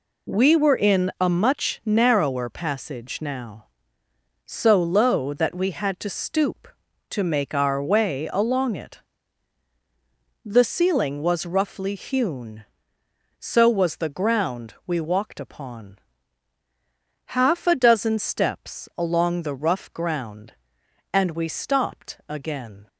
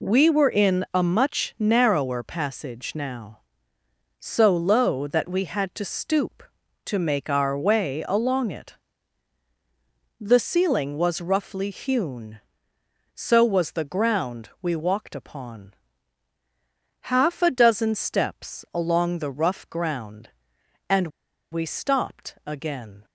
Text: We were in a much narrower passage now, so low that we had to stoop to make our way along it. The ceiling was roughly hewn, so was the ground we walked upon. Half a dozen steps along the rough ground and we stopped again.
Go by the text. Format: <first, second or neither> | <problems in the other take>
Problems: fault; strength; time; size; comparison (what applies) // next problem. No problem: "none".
first | pauses between "and" and "we"; at 21.1 s; 0.42 s long